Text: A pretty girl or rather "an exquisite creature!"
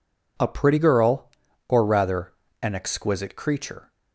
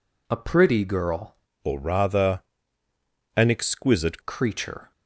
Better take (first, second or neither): first